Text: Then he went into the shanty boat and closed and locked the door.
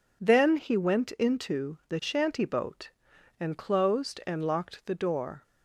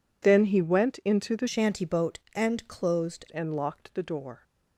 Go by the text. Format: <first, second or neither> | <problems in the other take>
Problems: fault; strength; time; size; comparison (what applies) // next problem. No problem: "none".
first | changes voice from "shanty" to "closed"; from 1.4 to 3.2 s; 1.8 s long